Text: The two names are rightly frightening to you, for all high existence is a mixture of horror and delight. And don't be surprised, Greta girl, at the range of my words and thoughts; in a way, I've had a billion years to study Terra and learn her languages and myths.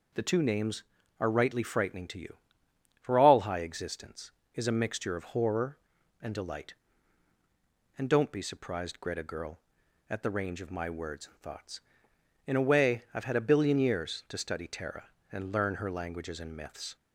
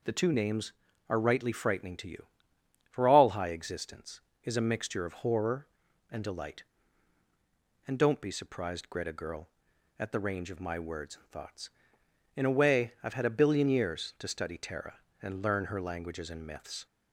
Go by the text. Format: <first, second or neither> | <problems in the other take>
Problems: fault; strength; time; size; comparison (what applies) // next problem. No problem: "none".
neither | none